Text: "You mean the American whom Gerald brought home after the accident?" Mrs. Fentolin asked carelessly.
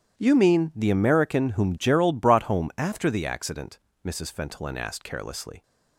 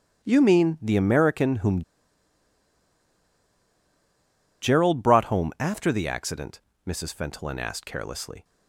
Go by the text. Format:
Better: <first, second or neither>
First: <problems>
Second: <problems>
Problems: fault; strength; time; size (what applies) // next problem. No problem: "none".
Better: first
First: starts louder than the rest; strong; until 1.2 s; 10.5 dB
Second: starts louder than the rest; strong; until 1.2 s; 10 dB // pauses between "whom" and "Gerald"; strong; at 1.8 s; 2.7 s long